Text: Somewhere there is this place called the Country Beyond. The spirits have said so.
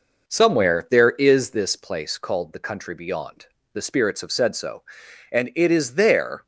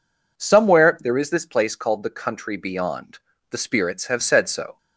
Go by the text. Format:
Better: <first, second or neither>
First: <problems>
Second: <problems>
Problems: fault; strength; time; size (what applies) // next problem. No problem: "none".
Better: second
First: goes on to say "And it is there"; noticeable; from 5.3 s on; 1.1 s long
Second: none